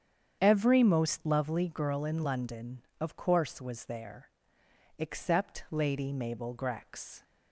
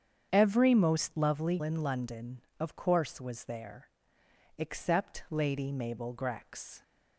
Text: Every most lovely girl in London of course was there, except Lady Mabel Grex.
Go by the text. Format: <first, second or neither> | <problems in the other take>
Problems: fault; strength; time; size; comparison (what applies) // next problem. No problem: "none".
first | starts louder than the rest; strong; until 1.3 s; 8 dB; strong in the first // skips "girl"; at 1.6 s